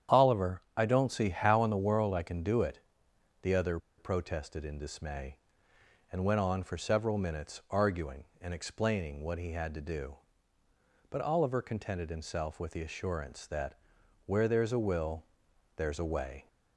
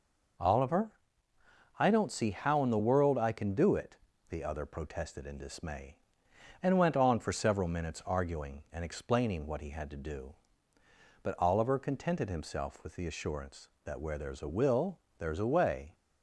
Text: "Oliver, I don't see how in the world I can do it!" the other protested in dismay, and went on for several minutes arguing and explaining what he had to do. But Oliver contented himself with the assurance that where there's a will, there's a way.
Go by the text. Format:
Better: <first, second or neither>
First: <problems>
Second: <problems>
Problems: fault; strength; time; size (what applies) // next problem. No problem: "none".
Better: second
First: starts louder than the rest; strong; until 1.2 s; 9 dB // pauses between "other" and "protested"; slight; at 3.7 s; 0.20 s long // pauses between "that" and "where"; noticeable; at 13.7 s; 0.50 s long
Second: none